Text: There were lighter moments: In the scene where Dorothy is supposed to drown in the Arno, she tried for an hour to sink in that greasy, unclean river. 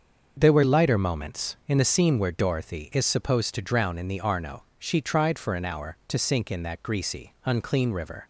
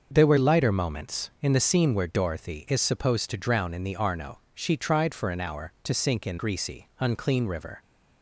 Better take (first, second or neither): first